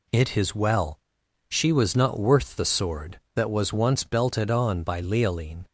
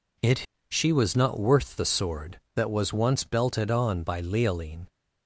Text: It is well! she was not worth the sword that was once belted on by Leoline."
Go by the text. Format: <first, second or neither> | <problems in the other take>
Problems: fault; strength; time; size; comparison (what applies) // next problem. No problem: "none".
first | skips "is well"; at 0.5 s